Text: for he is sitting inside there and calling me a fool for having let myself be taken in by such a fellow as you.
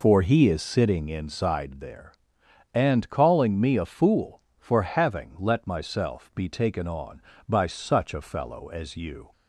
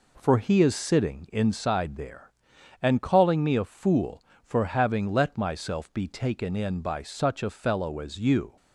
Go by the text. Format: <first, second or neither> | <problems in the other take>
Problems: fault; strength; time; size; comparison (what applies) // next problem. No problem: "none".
second | says "on" for "in"; at 6.8 s